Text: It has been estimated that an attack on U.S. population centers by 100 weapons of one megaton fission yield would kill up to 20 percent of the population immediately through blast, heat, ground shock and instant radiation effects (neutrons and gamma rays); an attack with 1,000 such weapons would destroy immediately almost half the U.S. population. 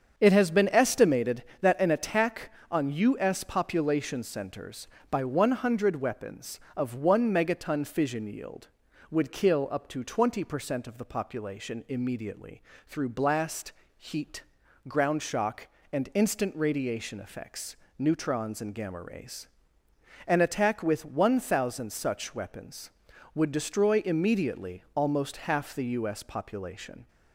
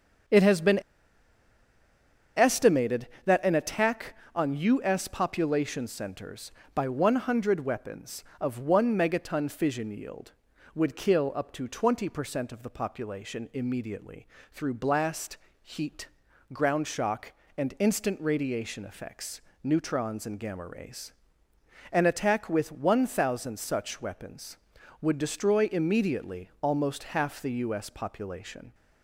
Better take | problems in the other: first | starts louder than the rest; strong; until 2.8 s; 7.5 dB; strong in the first // pauses between "been" and "estimated"; strong; at 0.8 s; 1.5 s long // pauses between "immediately" and "through"; slight; at 14.2 s; 0.26 s long; slight in the first

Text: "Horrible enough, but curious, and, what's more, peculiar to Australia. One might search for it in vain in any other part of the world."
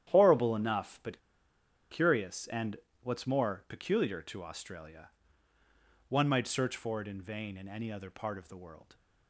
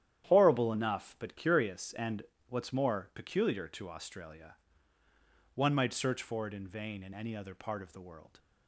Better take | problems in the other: second | starts louder than the rest; strong; until 1.0 s; 10.5 dB; strong in the second // pauses between "but" and "curious"; noticeable; at 1.2 s; 0.70 s long

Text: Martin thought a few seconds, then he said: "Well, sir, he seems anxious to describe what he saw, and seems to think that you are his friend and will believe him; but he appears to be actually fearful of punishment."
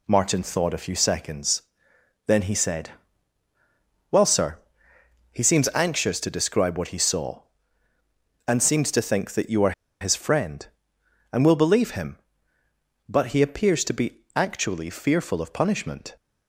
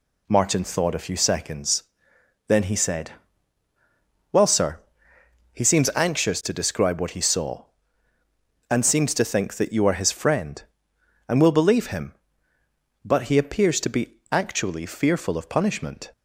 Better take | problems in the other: second | pauses between "are" and "his"; slight; at 9.7 s; 0.28 s long

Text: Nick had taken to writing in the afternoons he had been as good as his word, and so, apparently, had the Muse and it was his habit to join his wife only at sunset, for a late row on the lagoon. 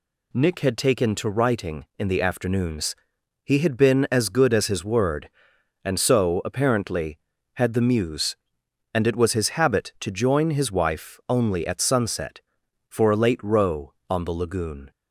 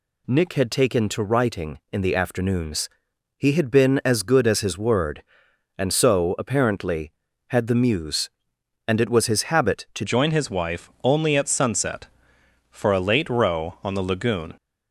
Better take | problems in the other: first | pauses between "afternoons" and "he"; noticeable; at 2.8 s; 0.48 s long; noticeable in the first // changes voice at "join"; from 10.0 s on; 4.5 s long // pauses between "wife" and "only"; slight; at 10.8 s; 0.16 s long

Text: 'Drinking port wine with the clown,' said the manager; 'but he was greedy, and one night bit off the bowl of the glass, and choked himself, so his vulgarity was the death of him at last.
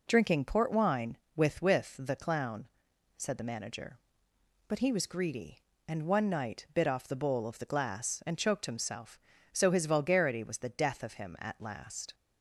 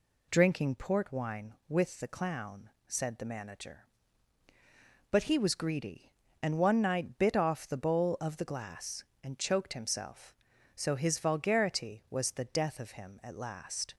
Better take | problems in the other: second | says "with" twice; at 1.6 s

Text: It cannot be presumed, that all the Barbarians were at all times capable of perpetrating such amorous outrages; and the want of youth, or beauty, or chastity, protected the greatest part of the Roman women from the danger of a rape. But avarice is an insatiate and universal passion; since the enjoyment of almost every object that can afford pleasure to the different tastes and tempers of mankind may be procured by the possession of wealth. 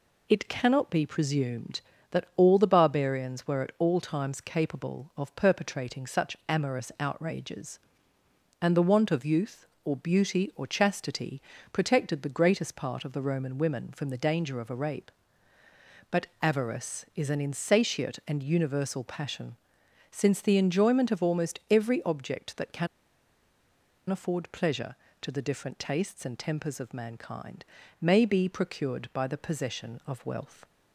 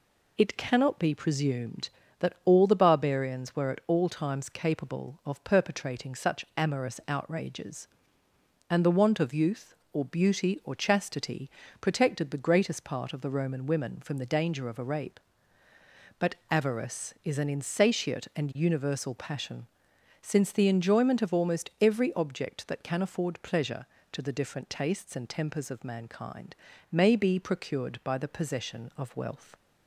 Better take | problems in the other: second | pauses between "can" and "afford"; at 22.8 s; 1.2 s long // pauses between "mankind" and "may"; slight; at 27.6 s; 0.34 s long; slight in the second

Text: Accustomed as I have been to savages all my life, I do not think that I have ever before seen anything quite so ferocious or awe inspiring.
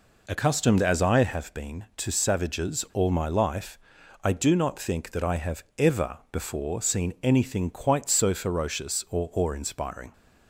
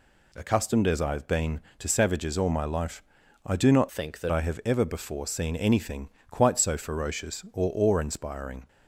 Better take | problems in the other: first | changes voice from "think" to "that"; from 3.8 to 4.3 s; 0.5 s long // pauses between "anything" and "quite"; slight; at 6.0 s; 0.20 s long

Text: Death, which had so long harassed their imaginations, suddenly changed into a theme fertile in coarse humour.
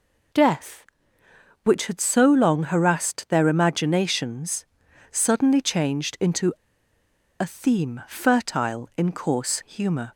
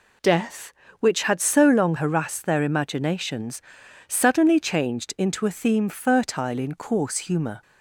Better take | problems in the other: second | pauses between "into" and "a"; noticeable; at 6.5 s; 0.86 s long

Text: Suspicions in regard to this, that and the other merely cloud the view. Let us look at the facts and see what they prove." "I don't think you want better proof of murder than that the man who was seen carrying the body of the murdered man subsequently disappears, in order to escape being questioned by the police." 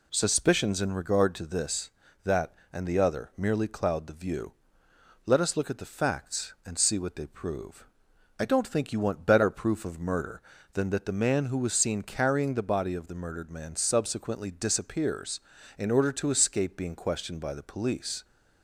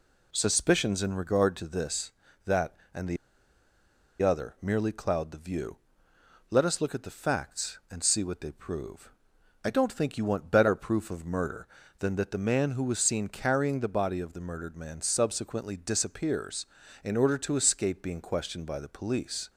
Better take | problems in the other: first | pauses between "the" and "other"; at 3.1 s; 1.0 s long

